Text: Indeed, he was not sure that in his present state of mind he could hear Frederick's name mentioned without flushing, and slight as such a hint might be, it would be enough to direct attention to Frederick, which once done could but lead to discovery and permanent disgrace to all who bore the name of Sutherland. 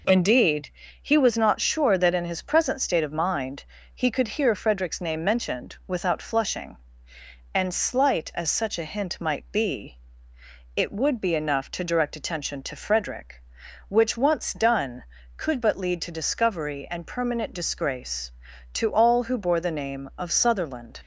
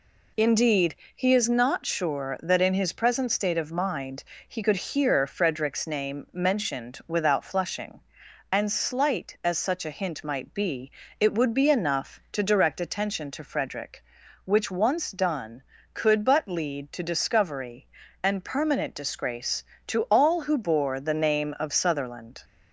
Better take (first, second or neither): first